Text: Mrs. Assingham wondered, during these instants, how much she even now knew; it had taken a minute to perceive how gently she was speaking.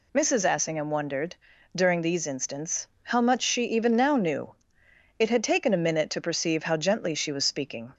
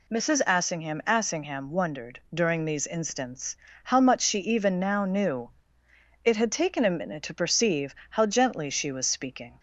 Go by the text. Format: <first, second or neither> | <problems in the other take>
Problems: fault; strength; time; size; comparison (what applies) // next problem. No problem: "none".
first | says "Assingham" twice; at 1.0 s // pauses between "perceive" and "how"; slight; at 7.9 s; 0.18 s long